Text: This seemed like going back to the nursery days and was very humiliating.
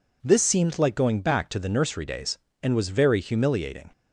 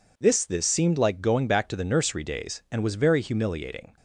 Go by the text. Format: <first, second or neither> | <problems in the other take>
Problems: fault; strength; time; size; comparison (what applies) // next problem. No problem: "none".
first | says "This" twice; at 0.4 s